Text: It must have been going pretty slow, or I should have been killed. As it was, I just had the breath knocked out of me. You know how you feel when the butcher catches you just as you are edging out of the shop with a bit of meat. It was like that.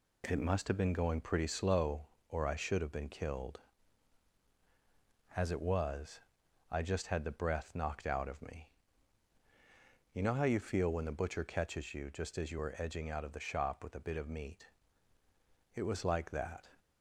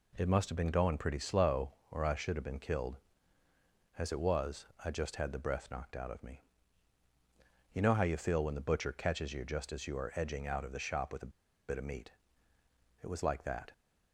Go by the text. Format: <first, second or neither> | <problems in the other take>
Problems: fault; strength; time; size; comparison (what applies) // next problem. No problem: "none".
first | pauses between "a" and "bit"; at 11.3 s; 0.37 s long